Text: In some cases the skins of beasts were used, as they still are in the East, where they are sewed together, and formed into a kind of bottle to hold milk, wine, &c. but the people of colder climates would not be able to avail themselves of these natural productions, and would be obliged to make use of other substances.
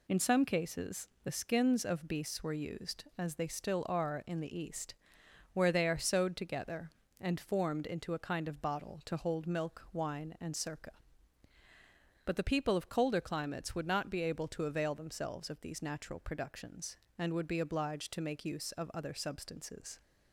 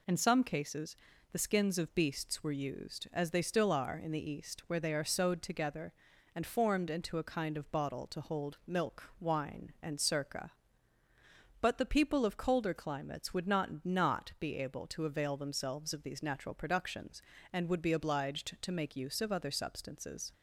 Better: first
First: pauses between "cases" and "the"; slight; at 1.0 s; 0.16 s long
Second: pauses between "cases" and "the"; slight; at 0.9 s; 0.36 s long // says "not" twice; at 13.8 s

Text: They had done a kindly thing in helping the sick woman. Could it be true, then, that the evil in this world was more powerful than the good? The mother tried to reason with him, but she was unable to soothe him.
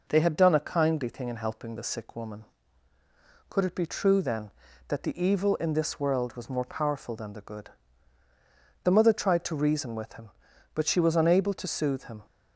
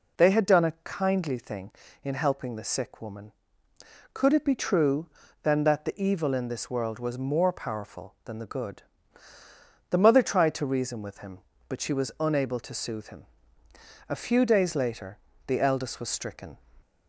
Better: first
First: none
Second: goes on to say "A few days later the eldest was stricken"; strong; from 14.0 s on; 2.5 s long

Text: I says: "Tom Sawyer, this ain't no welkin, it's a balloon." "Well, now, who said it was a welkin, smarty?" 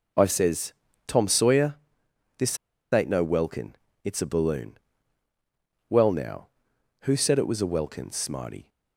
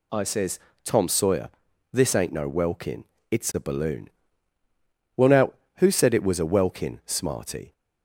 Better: second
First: pauses between "this" and "ain't"; slight; at 2.5 s; 0.35 s long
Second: none

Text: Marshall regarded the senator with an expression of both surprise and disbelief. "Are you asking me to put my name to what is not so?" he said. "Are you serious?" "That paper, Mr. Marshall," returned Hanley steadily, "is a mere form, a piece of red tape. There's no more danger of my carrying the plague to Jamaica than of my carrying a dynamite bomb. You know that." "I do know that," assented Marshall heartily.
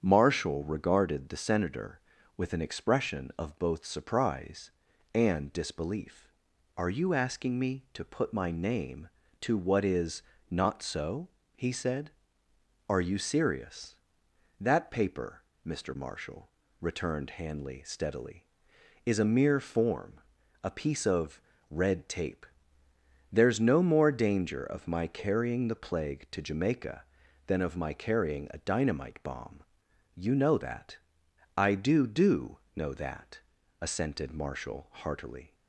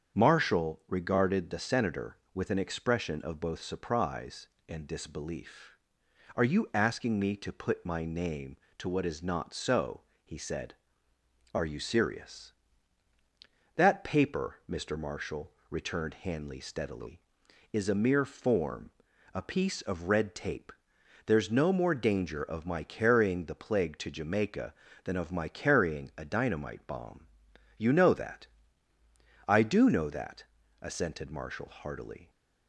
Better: second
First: starts louder than the rest; strong; until 1.0 s; 8 dB // pauses between "is" and "not"; slight; at 10.2 s; 0.26 s long // pauses between "of" and "red"; slight; at 21.3 s; 0.30 s long // says "do" twice; at 32.0 s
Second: starts louder than the rest; strong; until 1.2 s; 7.5 dB

